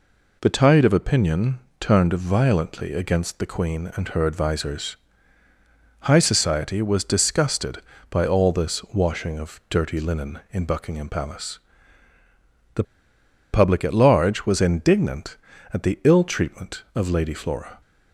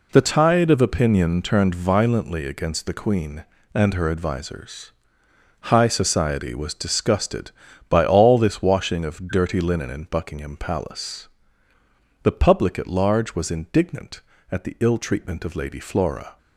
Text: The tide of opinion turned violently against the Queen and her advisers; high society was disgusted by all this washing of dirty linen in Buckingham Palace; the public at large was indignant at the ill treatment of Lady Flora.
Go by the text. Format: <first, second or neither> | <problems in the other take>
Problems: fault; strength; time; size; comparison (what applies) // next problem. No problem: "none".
second | pauses between "opinion" and "turned"; slight; at 1.5 s; 0.20 s long // pauses between "the" and "public"; noticeable; at 12.8 s; 0.69 s long